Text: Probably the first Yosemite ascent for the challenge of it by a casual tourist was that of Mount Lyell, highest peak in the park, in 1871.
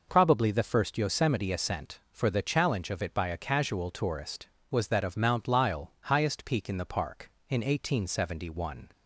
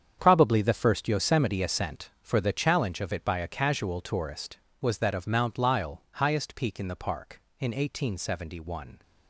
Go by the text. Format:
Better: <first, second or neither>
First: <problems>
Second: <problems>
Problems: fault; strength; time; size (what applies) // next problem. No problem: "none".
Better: first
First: none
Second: gets quieter; strong; throughout; 12 dB